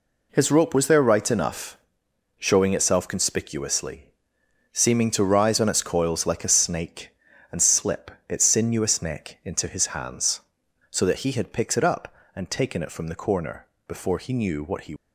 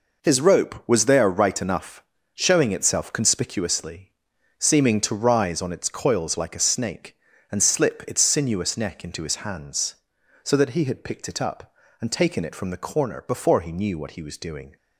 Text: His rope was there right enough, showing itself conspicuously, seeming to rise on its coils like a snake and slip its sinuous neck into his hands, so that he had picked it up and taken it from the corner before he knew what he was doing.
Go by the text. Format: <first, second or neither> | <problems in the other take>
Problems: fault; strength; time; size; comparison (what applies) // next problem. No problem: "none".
second | pauses between "slip" and "its"; slight; at 8.1 s; 0.16 s long // pauses between "corner" and "before"; slight; at 13.6 s; 0.22 s long // stops before "was doing"; at 14.9 s